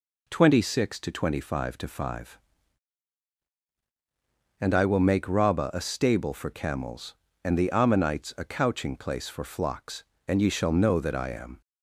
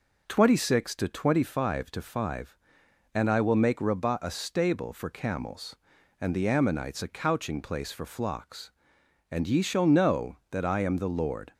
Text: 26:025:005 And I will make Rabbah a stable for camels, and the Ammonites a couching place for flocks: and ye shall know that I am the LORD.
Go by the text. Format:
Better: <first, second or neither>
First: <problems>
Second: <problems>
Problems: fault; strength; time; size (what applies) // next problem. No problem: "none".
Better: second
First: stops before "the LORD"; at 11.6 s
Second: none